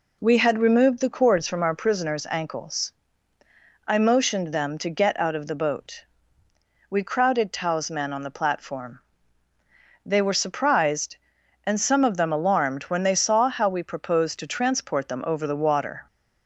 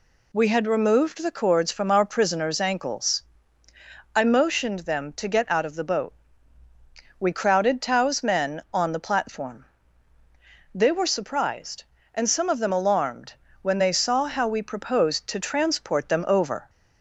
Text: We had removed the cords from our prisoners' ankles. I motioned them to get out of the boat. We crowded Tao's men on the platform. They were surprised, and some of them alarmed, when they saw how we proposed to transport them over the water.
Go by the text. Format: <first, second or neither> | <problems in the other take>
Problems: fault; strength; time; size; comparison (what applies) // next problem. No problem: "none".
first | stops before "the water"; at 16.6 s